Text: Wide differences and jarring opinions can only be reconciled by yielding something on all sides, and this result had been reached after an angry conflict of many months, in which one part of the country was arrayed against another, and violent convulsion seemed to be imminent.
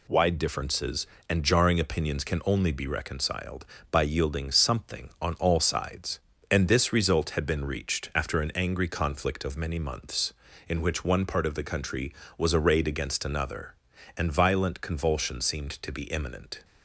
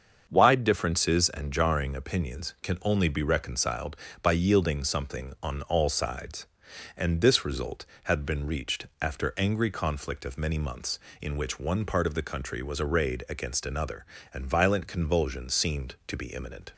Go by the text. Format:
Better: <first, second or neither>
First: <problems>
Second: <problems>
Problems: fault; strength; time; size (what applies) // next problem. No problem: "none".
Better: first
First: none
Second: starts louder than the rest; until 1.2 s; 7 dB // skips "an"; at 9.3 s